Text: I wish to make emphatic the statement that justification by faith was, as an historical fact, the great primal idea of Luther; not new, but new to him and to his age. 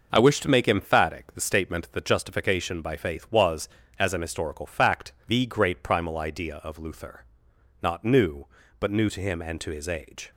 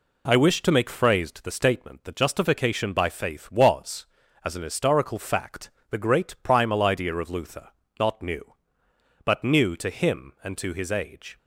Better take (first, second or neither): first